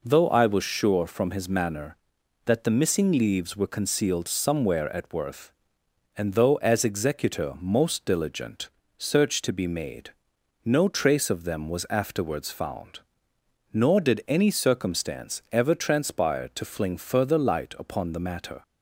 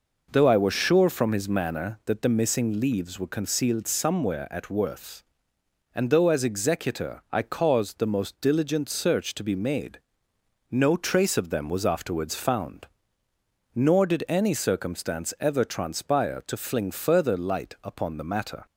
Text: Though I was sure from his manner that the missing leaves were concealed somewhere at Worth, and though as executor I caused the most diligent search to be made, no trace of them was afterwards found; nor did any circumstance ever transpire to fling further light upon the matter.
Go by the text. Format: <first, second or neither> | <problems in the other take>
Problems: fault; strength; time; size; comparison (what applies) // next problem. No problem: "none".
second | skips "I caused the"; at 7.5 s // pauses between "diligent" and "search"; slight; at 8.6 s; 0.28 s long